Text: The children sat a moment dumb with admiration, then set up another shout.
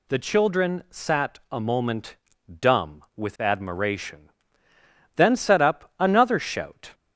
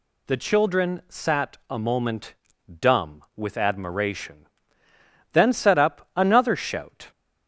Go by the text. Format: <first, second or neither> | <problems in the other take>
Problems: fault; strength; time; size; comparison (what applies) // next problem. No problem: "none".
neither | pauses between "moment" and "dumb"; the same in both